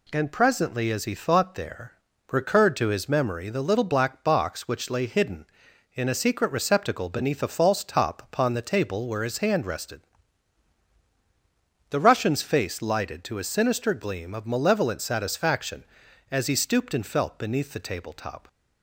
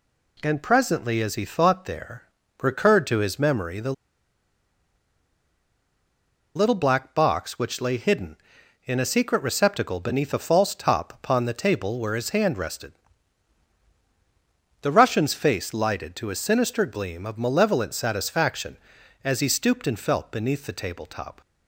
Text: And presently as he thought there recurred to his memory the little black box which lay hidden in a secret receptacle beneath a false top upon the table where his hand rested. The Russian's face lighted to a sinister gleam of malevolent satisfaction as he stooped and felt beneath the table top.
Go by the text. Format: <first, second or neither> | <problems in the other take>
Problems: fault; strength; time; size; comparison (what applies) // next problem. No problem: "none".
first | pauses between "there" and "recurred"; at 2.2 s; 0.38 s long; also in the first // pauses between "the" and "little"; strong; at 3.9 s; 2.6 s long